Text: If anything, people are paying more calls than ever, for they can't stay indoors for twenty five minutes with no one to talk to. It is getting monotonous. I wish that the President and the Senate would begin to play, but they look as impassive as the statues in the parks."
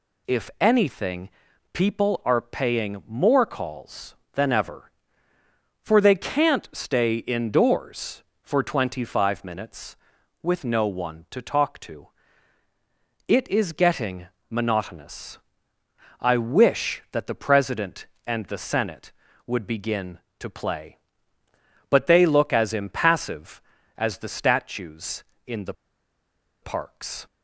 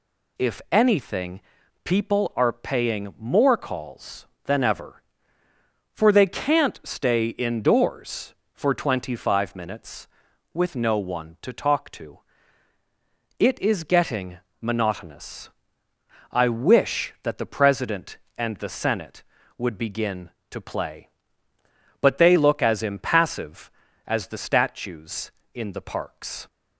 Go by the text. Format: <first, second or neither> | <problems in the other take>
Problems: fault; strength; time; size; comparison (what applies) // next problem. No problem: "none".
second | pauses between "getting" and "monotonous"; slight; at 14.2 s; 0.22 s long; slight in the second // pauses between "the" and "parks"; noticeable; at 25.7 s; 0.89 s long